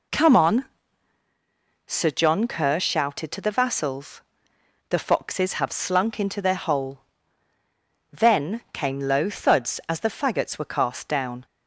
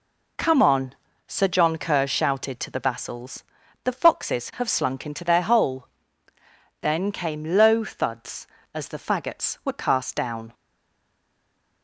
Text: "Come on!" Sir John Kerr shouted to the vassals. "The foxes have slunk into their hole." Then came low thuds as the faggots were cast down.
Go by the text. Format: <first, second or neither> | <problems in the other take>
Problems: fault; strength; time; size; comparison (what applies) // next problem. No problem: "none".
first | stays silent after the last word; noticeable; from 10.5 s on; 1.3 s long